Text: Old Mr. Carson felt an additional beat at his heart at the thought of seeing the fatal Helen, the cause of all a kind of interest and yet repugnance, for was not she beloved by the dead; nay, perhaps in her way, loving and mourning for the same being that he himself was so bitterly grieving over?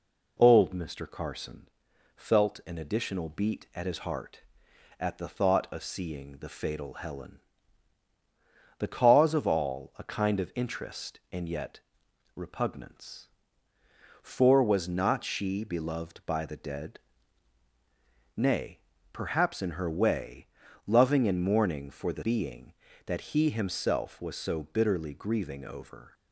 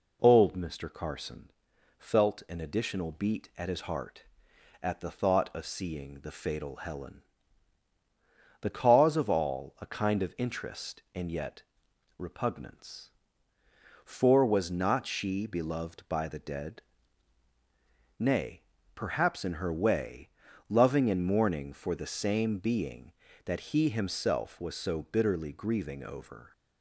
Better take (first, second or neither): second